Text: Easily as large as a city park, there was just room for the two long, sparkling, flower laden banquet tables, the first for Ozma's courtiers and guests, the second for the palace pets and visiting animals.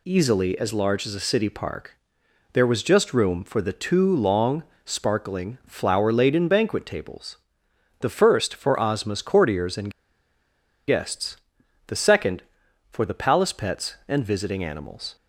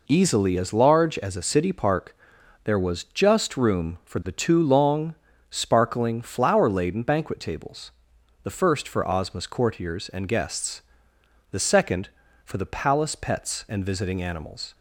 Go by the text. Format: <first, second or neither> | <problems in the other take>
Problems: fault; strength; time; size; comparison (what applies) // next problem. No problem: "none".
second | pauses between "and" and "guests"; noticeable; at 9.8 s; 0.98 s long